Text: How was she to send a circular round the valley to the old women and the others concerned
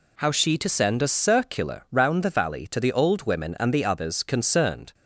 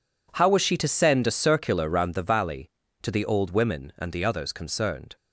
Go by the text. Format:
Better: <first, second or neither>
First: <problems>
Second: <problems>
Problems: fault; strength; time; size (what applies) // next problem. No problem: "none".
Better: second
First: skips "was"; at 0.3 s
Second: none